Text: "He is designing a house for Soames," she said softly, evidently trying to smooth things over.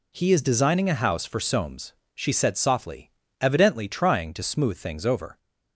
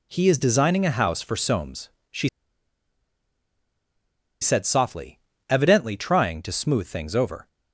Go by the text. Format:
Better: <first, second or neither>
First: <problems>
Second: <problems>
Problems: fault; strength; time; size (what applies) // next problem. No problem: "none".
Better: first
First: none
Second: pauses between "she" and "said"; strong; at 2.2 s; 2.1 s long